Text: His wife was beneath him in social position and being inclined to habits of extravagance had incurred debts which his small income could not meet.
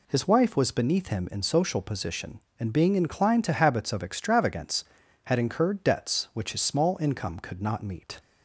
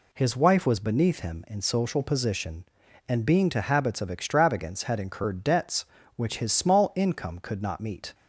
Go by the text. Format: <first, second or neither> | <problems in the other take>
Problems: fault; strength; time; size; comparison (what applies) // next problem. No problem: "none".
first | skips "inclined"; at 3.4 s